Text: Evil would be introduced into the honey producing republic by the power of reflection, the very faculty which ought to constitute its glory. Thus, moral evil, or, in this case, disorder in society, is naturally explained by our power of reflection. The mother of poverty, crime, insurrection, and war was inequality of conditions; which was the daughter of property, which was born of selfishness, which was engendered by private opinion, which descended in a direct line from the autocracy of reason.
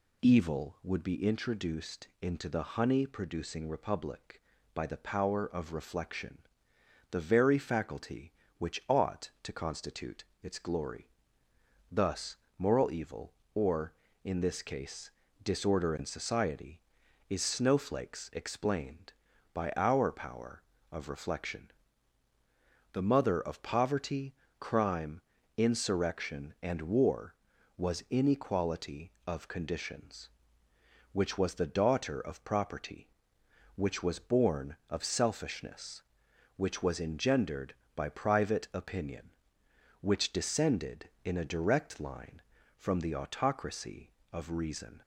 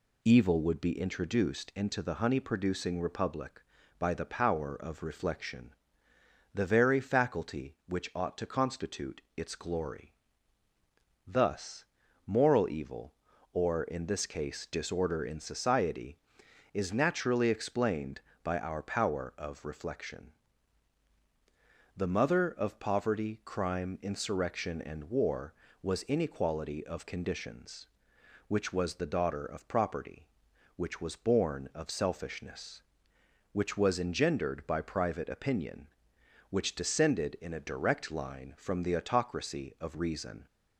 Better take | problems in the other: second | pauses between "constitute" and "its"; slight; at 10.2 s; 0.20 s long // says "snowflakes" for "naturally"; at 17.4 s

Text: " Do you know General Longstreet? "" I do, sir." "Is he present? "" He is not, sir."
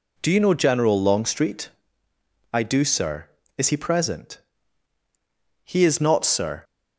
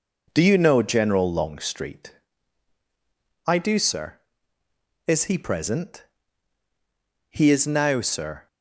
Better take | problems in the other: first | starts louder than the rest; until 1.3 s; 6 dB // says "now" for "not"; at 7.6 s

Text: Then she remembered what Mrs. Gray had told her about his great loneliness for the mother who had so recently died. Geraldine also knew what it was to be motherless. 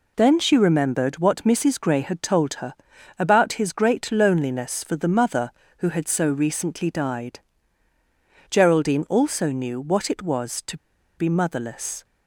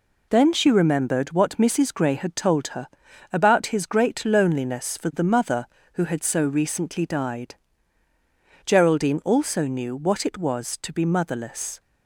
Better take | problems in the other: second | pauses between "her" and "about"; at 2.7 s; 0.44 s long; also in the second // pauses between "to" and "be"; at 10.7 s; 0.40 s long

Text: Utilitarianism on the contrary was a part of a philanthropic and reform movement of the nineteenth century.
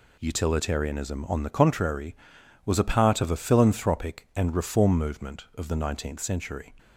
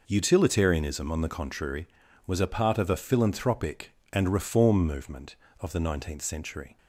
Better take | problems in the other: neither | none

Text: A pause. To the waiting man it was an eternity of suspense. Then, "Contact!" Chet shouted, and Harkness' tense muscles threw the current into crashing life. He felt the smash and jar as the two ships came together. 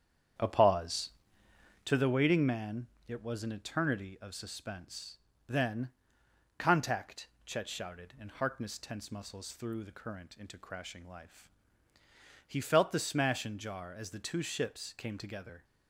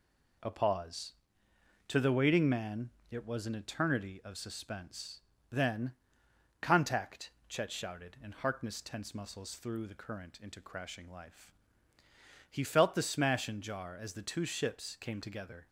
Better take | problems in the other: second | starts louder than the rest; strong; until 2.0 s; 8.5 dB // pauses between "man" and "it"; slight; at 2.8 s; 0.20 s long; slight in the second

